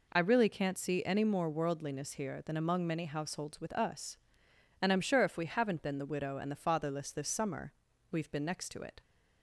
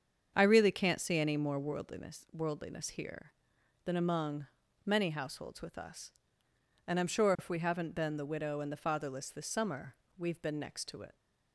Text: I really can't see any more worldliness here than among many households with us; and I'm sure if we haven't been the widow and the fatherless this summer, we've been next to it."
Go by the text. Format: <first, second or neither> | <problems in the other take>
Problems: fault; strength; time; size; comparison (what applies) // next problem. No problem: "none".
first | starts louder than the rest; strong; until 1.3 s; 7.5 dB // says "worldliness" twice; at 2.3 s // pauses between "among" and "many"; at 4.4 s; 0.38 s long